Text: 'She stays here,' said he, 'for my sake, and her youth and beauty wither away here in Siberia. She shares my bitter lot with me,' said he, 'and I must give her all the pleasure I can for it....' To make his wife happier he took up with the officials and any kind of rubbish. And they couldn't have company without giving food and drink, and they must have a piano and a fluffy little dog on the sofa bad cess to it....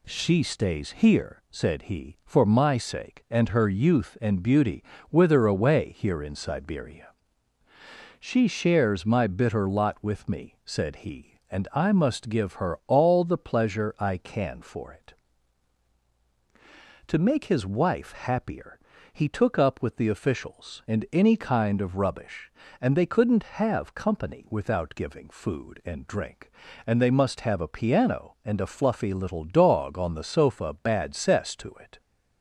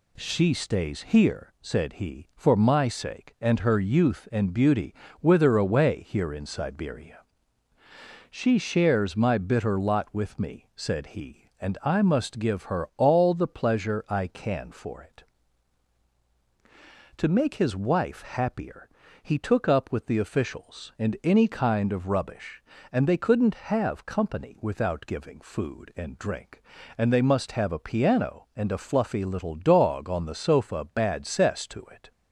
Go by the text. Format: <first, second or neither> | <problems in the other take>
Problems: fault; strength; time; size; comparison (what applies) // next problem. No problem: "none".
neither | pauses between "beauty" and "wither"; slight; the same in both // pauses between "happier" and "he"; slight; the same in both